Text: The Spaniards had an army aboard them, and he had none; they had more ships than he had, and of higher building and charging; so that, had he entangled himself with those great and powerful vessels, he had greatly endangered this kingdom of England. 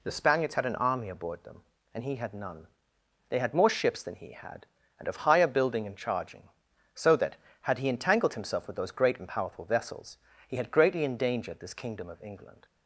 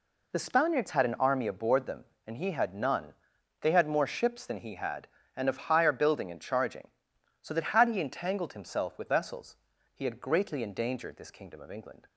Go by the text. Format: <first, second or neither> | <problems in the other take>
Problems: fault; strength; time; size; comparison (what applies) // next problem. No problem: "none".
first | skips "those great and powerful"; at 9.0 s